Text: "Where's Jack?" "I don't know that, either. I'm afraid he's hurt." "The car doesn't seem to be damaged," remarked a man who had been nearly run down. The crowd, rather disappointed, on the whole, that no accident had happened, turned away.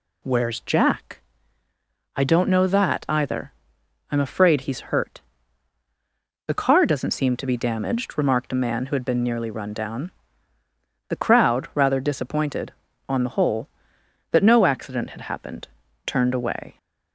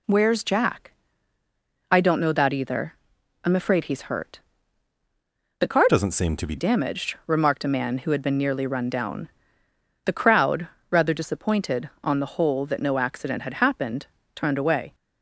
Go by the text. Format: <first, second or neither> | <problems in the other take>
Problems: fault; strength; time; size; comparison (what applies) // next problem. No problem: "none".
first | changes voice from "doesn't" to "be"; from 5.8 to 6.5 s; 0.7 s long